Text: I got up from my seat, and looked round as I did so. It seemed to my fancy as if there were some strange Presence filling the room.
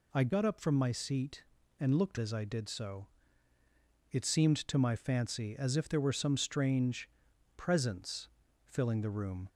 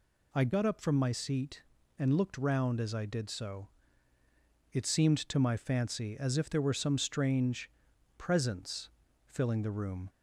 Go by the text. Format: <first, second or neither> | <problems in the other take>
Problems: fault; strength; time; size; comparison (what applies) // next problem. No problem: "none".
second | skips "round"; at 2.1 s // pauses between "strange" and "Presence"; noticeable; at 7.0 s; 0.48 s long; noticeable in the second // pauses between "Presence" and "filling"; at 8.2 s; 0.38 s long; also in the second